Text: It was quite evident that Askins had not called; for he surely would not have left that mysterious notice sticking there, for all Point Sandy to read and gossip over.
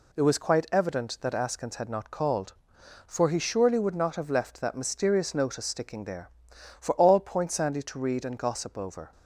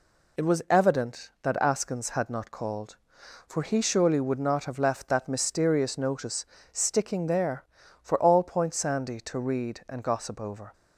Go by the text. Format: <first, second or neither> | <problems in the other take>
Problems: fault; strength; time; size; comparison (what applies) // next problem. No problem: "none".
first | skips "quite"; at 0.6 s // pauses between "notice" and "sticking"; slight; at 6.4 s; 0.26 s long